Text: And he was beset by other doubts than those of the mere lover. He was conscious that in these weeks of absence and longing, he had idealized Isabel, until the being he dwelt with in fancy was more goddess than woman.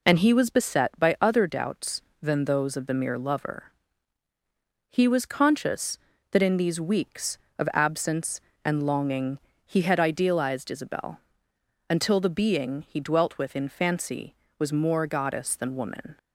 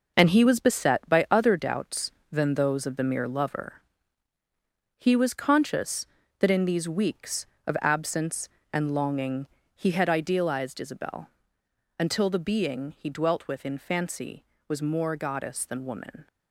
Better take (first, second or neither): first